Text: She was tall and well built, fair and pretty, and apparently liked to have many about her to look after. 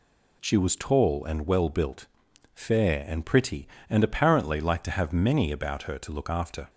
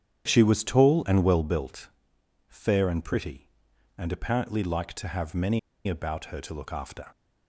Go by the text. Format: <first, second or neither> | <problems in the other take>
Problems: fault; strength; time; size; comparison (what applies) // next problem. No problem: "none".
first | starts louder than the rest; strong; until 1.2 s; 9 dB // pauses between "many" and "about"; slight; at 5.5 s; 0.28 s long